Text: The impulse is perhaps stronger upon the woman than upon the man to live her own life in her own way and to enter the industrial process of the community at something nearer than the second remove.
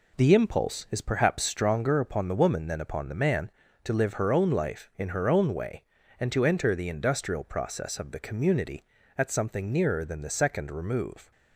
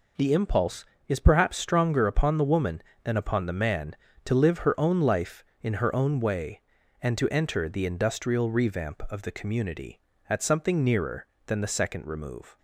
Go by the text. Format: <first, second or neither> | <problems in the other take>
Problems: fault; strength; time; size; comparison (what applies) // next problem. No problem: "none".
first | says "revamp" for "process"; at 8.4 s